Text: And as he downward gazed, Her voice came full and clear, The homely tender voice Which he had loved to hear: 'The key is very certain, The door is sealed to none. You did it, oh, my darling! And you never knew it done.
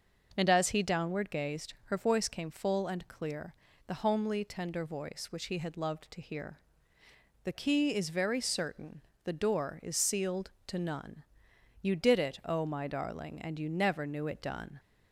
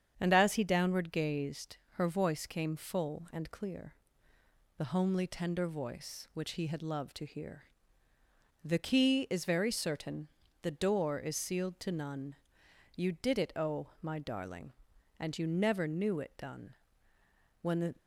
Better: first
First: starts louder than the rest; until 1.3 s; 6.5 dB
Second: starts louder than the rest; strong; until 1.1 s; 8 dB // goes on to say "When the"; slight; from 17.6 s on; 0.34 s long

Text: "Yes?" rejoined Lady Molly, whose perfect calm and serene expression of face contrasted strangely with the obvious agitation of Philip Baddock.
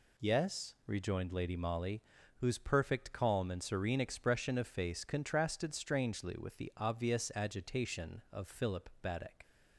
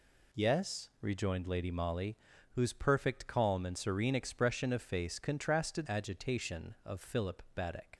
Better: first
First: none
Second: skips "strangely with the obvious"; at 5.8 s

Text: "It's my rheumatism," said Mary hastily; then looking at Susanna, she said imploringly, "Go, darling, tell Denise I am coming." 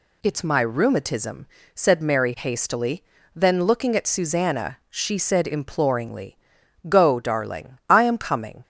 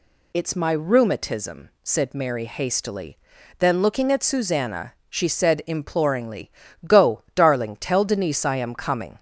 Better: second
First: skips "tell Denise"; at 7.8 s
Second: none

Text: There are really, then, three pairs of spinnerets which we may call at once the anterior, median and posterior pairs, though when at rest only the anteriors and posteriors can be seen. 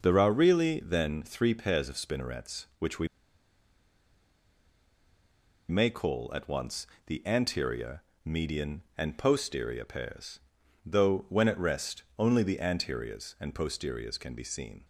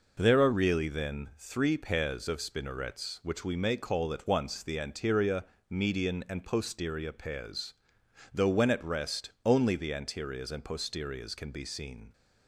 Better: second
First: pauses between "we" and "may"; strong; at 3.0 s; 2.6 s long // pauses between "once" and "the"; slight; at 6.8 s; 0.20 s long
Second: none

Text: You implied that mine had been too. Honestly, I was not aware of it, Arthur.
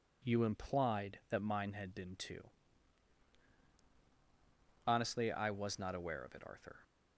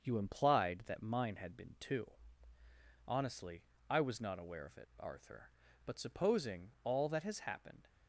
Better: first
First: none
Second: starts louder than the rest; until 1.0 s; 6.5 dB // goes on to say "But supposing all that has happened"; strong; from 5.8 s on; 2.0 s long

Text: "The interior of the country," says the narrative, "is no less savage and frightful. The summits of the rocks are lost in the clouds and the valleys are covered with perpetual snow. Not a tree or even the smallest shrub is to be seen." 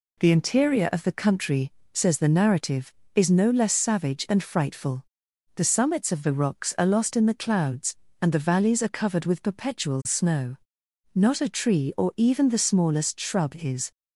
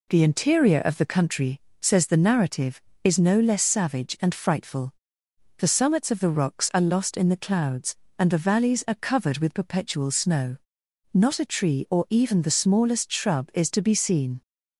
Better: second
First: stops before "to be seen"; at 13.9 s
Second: none

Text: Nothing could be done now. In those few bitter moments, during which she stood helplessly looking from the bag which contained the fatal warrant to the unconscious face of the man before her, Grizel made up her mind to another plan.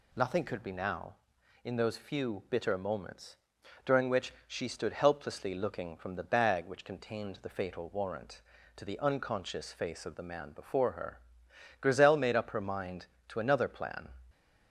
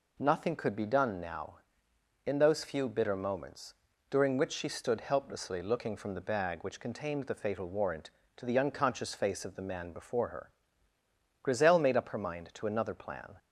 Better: second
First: skips "done"; at 0.7 s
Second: none

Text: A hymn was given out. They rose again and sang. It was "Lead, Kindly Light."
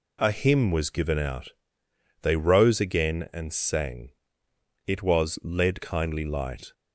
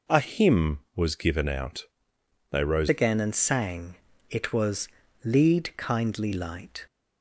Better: first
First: none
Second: changes voice at "again"; from 2.8 s on; 4.0 s long // pauses between "was" and "Lead"; slight; at 4.8 s; 0.36 s long

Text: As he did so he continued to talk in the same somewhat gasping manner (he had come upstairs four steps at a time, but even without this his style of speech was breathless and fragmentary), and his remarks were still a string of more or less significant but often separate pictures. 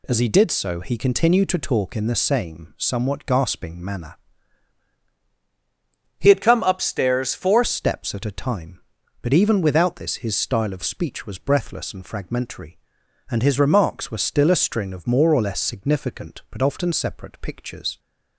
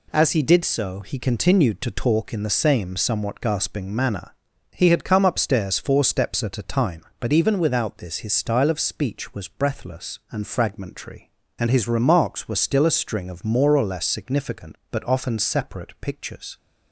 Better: second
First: changes voice from "had" to "four"; from 6.2 to 7.6 s; 1.4 s long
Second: none

